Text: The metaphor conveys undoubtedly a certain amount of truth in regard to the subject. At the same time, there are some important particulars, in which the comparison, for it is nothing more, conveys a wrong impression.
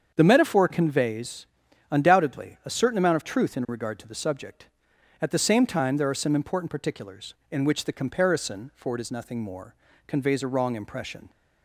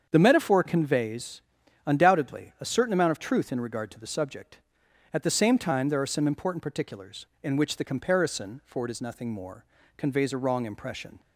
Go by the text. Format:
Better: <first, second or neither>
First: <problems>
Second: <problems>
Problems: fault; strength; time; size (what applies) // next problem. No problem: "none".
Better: neither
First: starts louder than the rest; strong; until 1.1 s; 7.5 dB // pauses between "conveys" and "undoubtedly"; at 1.4 s; 0.44 s long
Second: starts louder than the rest; strong; until 1.1 s; 7.5 dB // pauses between "conveys" and "undoubtedly"; at 1.4 s; 0.44 s long